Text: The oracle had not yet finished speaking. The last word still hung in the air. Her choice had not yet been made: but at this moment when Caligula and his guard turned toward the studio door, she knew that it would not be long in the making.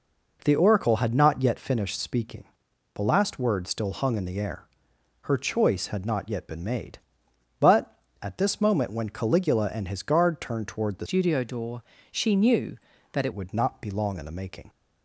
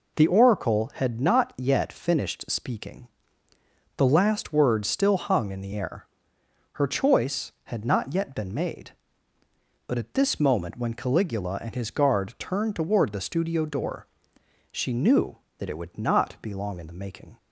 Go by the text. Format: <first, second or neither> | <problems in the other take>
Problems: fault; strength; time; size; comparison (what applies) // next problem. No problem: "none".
second | changes voice from "studio" to "it"; from 11.0 to 13.3 s; 2.3 s long